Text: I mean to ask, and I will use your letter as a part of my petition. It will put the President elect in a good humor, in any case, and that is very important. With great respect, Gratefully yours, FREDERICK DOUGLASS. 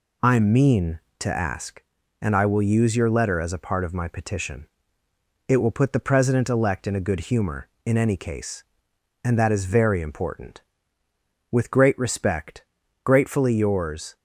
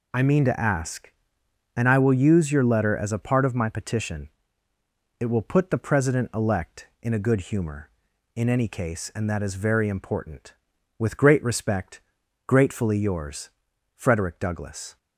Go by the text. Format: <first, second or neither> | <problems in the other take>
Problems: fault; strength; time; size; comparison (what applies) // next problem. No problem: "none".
second | stops before "FREDERICK DOUGLASS"; at 14.1 s